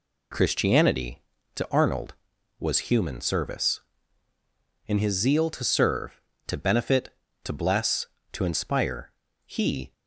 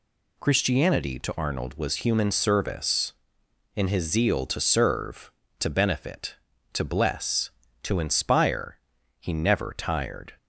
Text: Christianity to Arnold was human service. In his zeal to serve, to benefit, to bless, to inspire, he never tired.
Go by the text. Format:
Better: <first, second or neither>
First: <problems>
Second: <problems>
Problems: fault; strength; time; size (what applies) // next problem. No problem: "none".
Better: second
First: stops before "never tired"; at 9.9 s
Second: none